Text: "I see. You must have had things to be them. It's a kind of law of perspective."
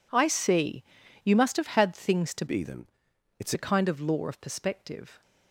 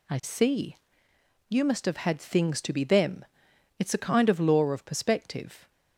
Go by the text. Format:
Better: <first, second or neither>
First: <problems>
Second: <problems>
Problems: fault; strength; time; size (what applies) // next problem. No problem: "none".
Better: second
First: changes voice from "be" to "It's"; from 2.4 to 3.5 s; 1.1 s long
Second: none